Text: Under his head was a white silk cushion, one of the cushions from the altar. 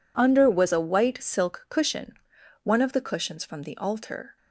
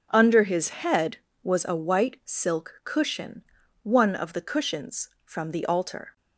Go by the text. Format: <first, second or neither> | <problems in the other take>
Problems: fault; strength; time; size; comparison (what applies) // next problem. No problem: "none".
second | skips "his head"; at 0.4 s